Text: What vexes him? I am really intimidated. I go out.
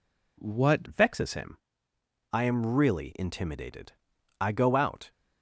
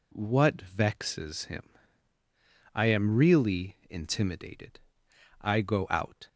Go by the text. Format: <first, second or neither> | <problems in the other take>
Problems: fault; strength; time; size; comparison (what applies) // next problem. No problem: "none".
second | changes voice at "vexes"; from 0.8 s on; 4.3 s long